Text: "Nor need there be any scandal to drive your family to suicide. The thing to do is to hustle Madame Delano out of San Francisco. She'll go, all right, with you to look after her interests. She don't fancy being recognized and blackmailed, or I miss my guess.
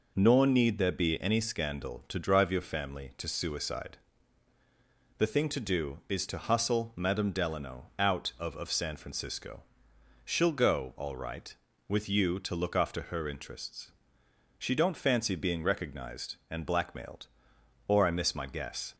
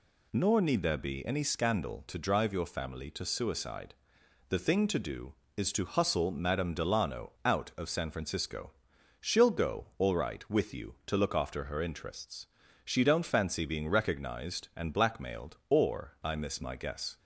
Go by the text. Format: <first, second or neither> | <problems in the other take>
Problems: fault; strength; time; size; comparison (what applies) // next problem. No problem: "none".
second | says "of" twice; at 8.5 s